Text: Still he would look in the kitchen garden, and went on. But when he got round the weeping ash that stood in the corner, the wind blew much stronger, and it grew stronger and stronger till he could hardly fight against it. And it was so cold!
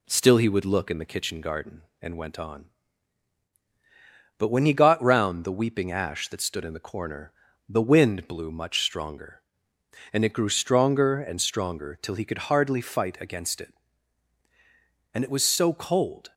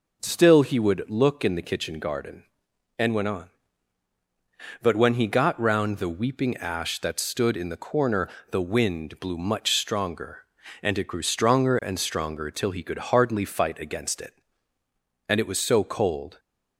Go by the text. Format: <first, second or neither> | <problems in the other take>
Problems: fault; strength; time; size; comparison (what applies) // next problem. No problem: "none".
neither | none